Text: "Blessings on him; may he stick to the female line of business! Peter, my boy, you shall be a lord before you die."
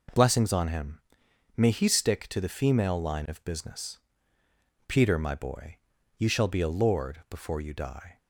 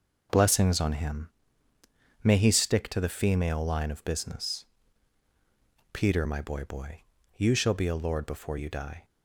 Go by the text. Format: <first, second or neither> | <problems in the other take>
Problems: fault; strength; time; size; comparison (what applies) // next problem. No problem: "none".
first | says "boy" twice; at 6.6 s